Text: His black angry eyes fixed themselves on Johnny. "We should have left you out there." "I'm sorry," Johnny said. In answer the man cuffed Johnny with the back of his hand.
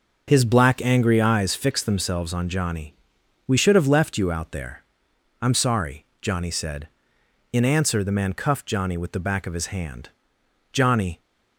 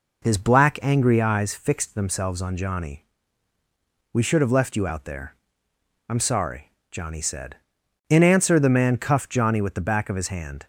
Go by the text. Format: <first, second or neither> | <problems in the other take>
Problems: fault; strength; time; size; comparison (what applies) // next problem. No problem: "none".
second | starts louder than the rest; noticeable; until 1.2 s; 6 dB // goes on to say "Johnny"; slight; from 10.7 s on; 0.46 s long